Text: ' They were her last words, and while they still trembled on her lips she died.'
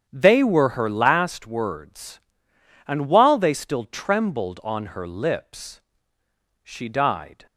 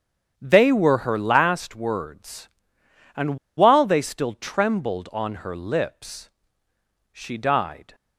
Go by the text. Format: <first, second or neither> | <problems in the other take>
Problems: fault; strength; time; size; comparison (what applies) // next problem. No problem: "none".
first | starts louder than the rest; strong; until 1.3 s; 8.5 dB; strong in the first // pauses between "and" and "while"; slight; at 3.3 s; 0.19 s long // pauses between "lips" and "she"; noticeable; at 6.2 s; 0.82 s long; noticeable in the first